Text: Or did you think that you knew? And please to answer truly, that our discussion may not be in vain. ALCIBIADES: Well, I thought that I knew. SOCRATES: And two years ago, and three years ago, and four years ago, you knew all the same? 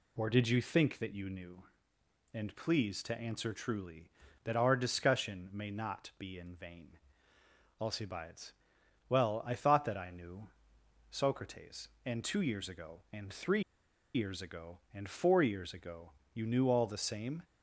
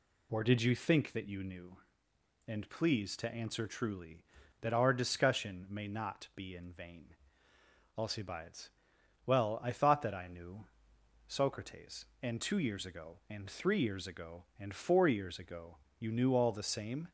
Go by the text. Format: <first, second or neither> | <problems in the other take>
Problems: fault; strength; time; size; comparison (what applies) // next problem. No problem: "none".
second | pauses between "three" and "years"; noticeable; at 13.6 s; 0.53 s long